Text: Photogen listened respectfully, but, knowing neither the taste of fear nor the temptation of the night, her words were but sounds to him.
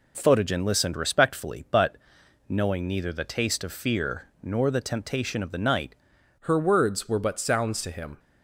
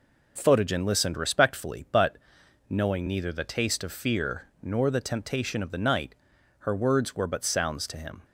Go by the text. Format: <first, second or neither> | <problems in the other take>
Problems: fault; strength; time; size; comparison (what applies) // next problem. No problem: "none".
second | changes voice at "her"; from 6.3 s on; 1.8 s long